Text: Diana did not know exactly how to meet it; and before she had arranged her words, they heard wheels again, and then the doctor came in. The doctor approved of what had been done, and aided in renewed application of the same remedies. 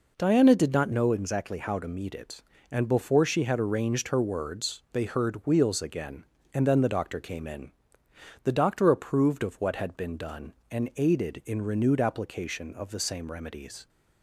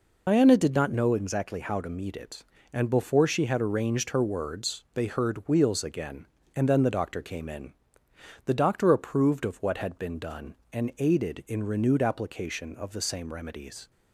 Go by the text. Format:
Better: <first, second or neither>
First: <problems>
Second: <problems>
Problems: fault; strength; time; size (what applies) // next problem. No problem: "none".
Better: first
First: none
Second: loses the start of "Diana"; at 0.2 s; 90 ms